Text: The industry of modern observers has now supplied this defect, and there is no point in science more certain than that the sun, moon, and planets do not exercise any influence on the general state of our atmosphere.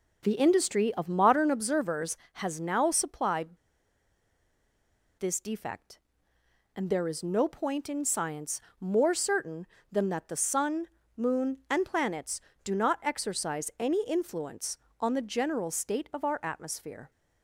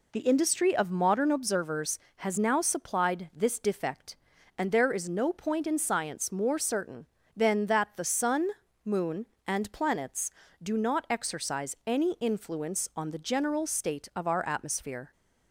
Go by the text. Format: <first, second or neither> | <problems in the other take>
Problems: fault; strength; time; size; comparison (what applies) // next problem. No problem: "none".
second | pauses between "supplied" and "this"; strong; at 3.5 s; 1.6 s long // pauses between "science" and "more"; slight; at 8.6 s; 0.18 s long